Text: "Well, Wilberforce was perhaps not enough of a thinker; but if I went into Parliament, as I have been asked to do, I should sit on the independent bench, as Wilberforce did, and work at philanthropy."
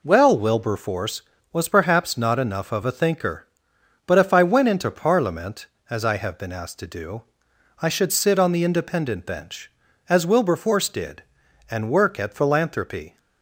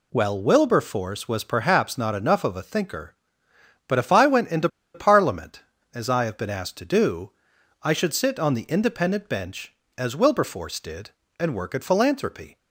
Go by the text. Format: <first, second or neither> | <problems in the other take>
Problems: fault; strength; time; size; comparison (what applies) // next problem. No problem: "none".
first | pauses between "into" and "Parliament"; slight; at 4.6 s; 0.27 s long